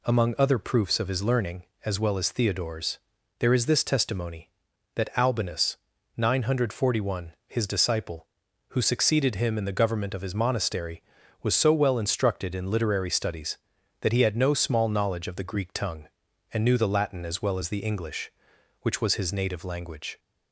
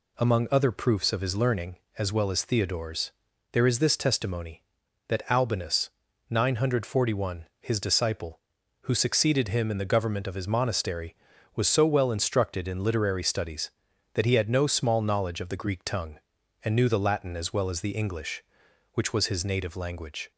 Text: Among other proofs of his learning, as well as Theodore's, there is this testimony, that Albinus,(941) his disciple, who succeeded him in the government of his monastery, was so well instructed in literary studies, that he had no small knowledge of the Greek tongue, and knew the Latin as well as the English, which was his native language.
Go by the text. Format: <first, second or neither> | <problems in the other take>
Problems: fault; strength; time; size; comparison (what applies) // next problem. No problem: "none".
neither | none